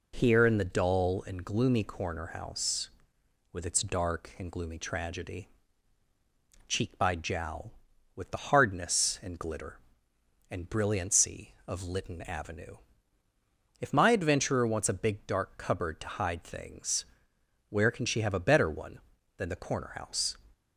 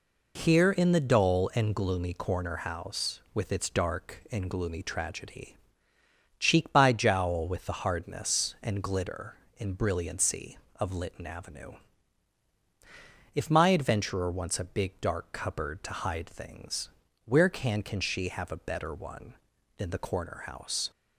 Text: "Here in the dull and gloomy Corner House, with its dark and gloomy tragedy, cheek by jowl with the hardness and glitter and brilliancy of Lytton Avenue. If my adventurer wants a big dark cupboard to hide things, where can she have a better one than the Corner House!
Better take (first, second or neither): first